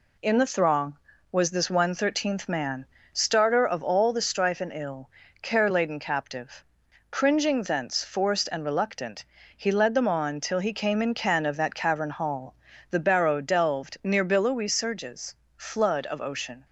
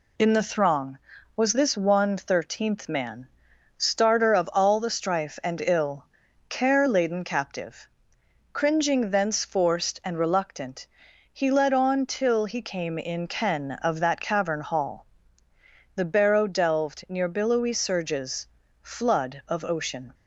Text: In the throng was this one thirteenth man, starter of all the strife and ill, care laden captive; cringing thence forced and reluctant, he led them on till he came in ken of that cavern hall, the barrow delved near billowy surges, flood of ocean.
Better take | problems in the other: first | skips "them"; at 11.7 s

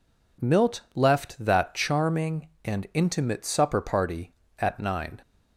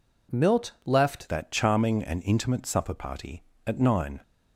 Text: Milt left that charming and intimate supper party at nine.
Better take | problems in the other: first | changes voice at "that"; from 1.3 s on; 2.9 s long

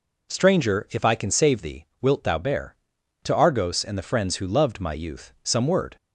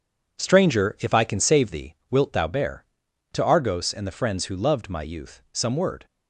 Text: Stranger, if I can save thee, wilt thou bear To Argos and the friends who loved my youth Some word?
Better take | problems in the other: first | gets quieter; strong; throughout; 9 dB

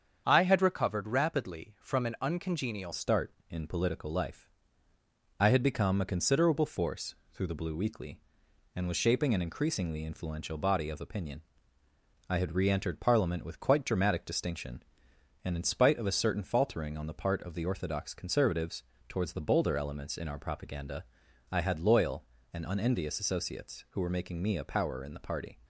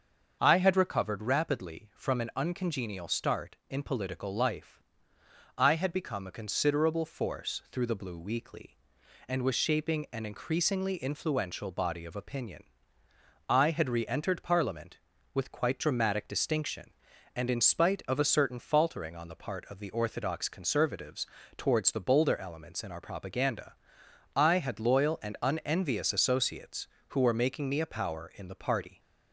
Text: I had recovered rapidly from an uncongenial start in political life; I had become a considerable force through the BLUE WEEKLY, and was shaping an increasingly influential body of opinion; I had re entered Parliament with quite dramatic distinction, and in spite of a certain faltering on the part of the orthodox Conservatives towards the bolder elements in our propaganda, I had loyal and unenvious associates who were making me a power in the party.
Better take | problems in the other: second | starts louder than the rest; strong; until 1.2 s; 7.5 dB; also in the second // changes voice at "start"; from 2.9 s on; 22.6 s long // pauses between "force" and "through"; slight; at 7.1 s; 0.18 s long // pauses between "Conservatives" and "towards"; slight; at 18.8 s; 0.24 s long; slight in the second

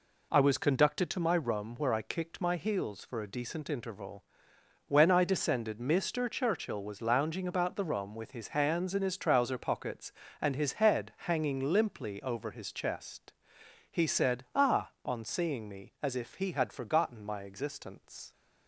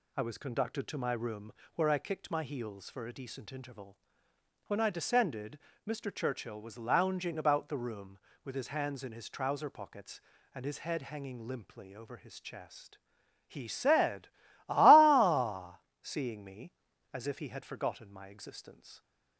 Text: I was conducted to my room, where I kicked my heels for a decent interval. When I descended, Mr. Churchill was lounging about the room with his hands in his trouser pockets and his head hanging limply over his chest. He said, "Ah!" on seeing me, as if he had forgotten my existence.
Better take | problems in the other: first | skips "on"; at 15.9 s

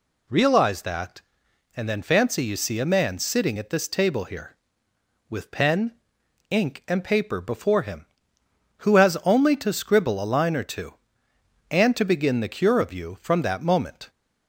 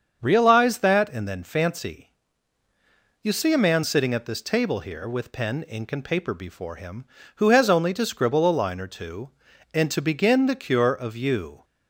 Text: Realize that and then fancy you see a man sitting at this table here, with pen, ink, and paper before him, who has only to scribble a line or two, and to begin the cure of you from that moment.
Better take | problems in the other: first | starts louder than the rest; until 1.2 s; 7 dB // pauses between "fancy" and "you"; at 2.0 s; 1.1 s long // stops before "from that moment"; at 11.6 s

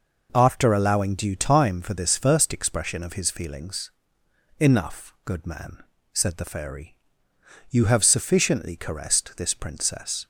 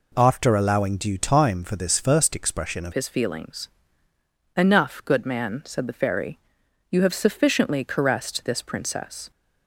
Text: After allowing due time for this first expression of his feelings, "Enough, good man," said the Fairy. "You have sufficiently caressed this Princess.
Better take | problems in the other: first | changes voice at "his"; from 2.9 s on; 6.4 s long

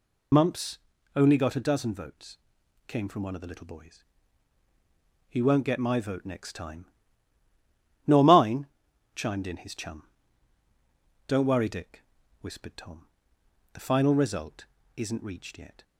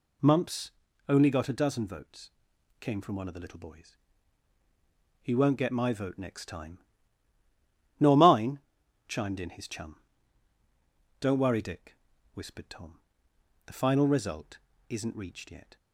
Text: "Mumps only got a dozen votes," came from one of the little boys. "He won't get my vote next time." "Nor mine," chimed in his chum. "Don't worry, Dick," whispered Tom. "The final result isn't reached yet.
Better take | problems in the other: second | loses the start of "Mumps"; at 0.3 s; 30 ms // pauses between "Mumps" and "only"; slight; at 0.7 s; 0.36 s long; slight in the second // pauses between "result" and "isn't"; slight; at 14.6 s; 0.32 s long; slight in the second

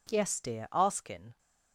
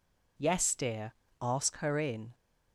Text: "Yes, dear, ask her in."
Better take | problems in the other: second | skips "her"; at 1.0 s

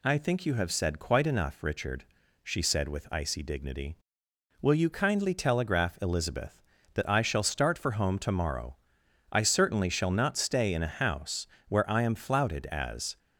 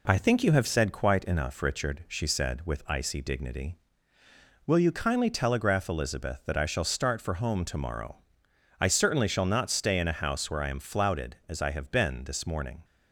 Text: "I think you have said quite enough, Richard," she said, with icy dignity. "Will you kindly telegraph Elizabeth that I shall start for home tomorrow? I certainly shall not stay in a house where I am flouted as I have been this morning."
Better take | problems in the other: second | pauses between "house" and "where"; slight; at 11.4 s; 0.22 s long // stops before "I have been this morning"; at 13.1 s

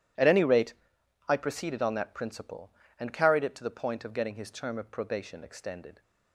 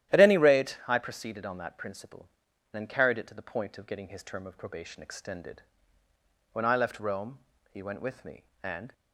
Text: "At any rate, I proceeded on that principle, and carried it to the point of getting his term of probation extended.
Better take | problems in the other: first | starts louder than the rest; strong; until 1.1 s; 12.5 dB // goes on to say "When I left Rome he went with me and"; strong; from 6.5 s on; 2.4 s long

